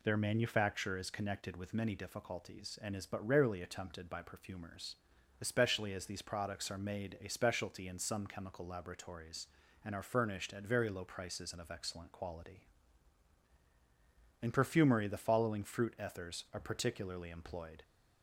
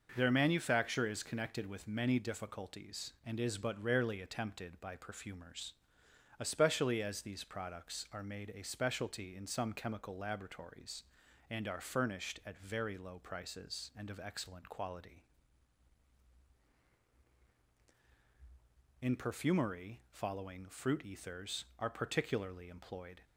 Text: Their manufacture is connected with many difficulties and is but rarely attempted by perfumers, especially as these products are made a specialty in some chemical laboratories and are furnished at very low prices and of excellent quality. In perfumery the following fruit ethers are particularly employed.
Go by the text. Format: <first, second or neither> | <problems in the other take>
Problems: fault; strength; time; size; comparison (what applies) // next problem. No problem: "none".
first | skips "the"; at 20.0 s